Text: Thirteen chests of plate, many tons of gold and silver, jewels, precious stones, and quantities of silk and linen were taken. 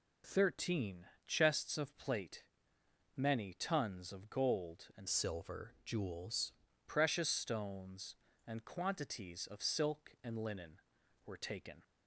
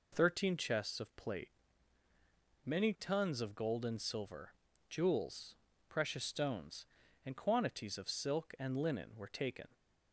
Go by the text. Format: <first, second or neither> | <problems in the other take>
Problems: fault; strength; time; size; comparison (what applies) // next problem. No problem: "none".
second | pauses between "Thirteen" and "chests"; slight; at 1.0 s; 0.22 s long // changes voice from "silver" to "jewels"; from 5.0 to 6.5 s; 1.5 s long